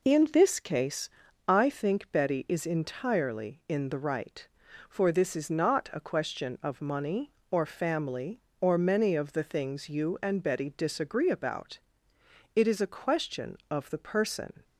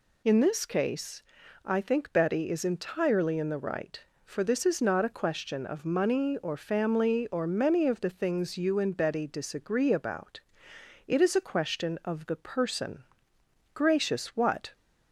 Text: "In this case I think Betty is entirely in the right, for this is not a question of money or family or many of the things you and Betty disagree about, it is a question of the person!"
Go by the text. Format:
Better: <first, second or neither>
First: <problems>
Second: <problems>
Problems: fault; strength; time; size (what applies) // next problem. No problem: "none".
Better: first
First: pauses between "case" and "I"; at 1.0 s; 0.38 s long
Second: pauses between "case" and "I"; at 1.2 s; 0.40 s long // goes on to say "Gracious what"; noticeable; from 13.7 s on; 1.0 s long